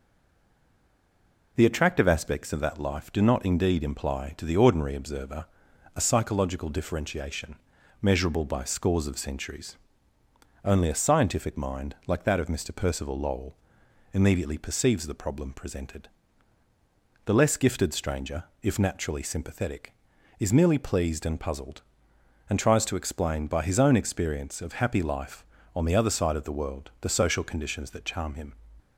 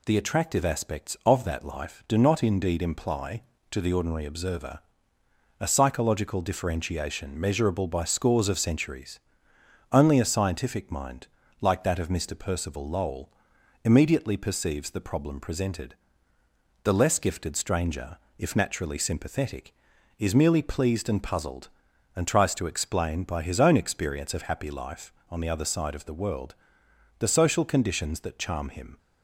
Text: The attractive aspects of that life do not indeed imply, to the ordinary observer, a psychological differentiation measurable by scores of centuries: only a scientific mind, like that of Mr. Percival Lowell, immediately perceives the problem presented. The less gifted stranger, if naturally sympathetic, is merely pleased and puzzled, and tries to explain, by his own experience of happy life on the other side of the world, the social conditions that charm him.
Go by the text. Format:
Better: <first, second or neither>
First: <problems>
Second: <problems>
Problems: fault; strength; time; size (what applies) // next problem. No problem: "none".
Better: second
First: stays silent before the first word; noticeable; until 1.5 s; 1.5 s long // pauses between "differentiation" and "measurable"; noticeable; at 7.5 s; 0.46 s long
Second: none